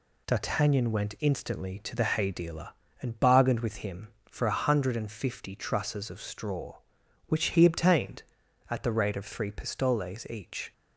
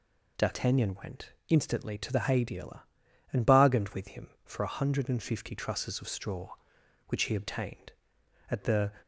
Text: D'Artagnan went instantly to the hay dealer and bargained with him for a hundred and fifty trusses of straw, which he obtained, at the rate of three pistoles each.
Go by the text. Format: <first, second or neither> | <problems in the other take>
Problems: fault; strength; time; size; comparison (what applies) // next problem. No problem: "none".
first | pauses between "went" and "instantly"; slight; at 1.3 s; 0.16 s long // stops before "rate of three pistoles each"; at 9.0 s